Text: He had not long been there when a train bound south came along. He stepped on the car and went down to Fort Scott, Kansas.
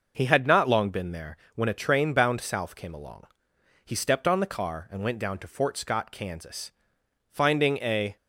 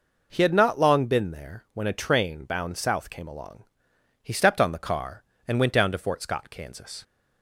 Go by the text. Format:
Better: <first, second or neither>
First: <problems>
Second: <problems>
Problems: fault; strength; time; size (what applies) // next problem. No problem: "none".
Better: second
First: pauses between "there" and "when"; slight; at 1.3 s; 0.20 s long // goes on to say "Finding a"; noticeable; from 7.2 s on; 0.86 s long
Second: none